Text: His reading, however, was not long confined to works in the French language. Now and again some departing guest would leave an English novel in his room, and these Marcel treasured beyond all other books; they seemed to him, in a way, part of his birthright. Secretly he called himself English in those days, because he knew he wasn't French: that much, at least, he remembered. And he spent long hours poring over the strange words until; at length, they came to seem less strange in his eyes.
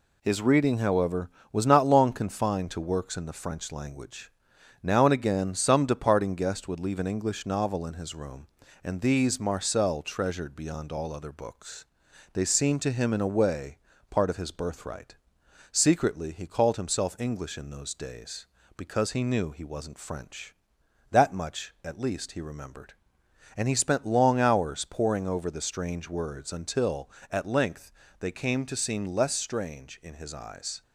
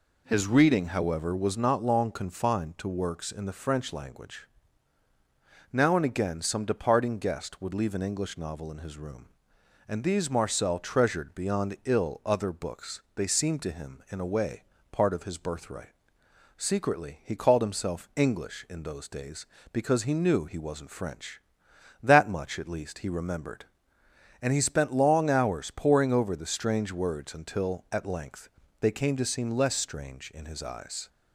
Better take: first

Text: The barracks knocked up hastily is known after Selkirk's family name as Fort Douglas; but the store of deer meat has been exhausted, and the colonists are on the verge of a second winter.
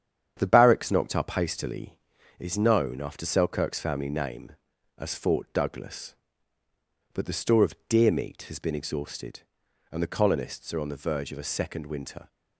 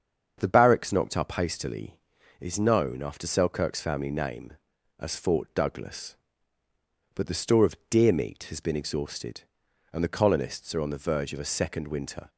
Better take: second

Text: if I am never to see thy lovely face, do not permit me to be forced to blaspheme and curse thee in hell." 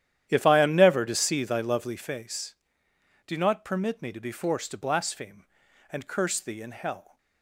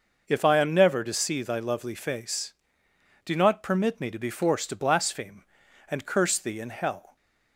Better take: second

